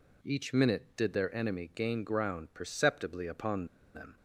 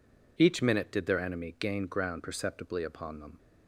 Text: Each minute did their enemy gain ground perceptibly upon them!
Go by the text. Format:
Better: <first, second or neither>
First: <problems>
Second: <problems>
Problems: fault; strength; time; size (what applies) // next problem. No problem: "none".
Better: second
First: pauses between "upon" and "them"; slight; at 3.6 s; 0.29 s long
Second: none